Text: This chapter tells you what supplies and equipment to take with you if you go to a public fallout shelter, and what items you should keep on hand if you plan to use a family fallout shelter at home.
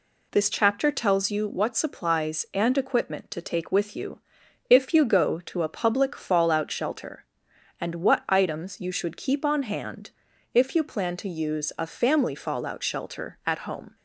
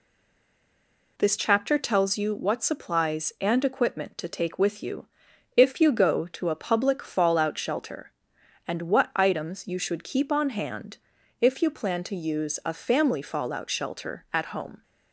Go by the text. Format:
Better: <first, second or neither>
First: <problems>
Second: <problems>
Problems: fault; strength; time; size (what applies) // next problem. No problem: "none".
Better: first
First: pauses between "you" and "if"; noticeable; at 4.1 s; 0.50 s long // pauses between "hand" and "if"; at 10.1 s; 0.42 s long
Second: stays silent before the first word; noticeable; until 1.1 s; 1.1 s long // pauses between "you" and "if"; noticeable; at 5.0 s; 0.50 s long // pauses between "hand" and "if"; at 10.9 s; 0.42 s long